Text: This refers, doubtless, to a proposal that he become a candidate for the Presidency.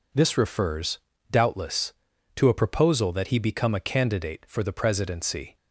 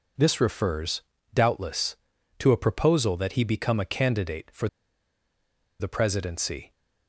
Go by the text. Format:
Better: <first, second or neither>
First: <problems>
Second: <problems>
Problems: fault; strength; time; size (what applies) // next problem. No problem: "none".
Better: first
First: none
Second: pauses between "for" and "the"; at 4.6 s; 1.1 s long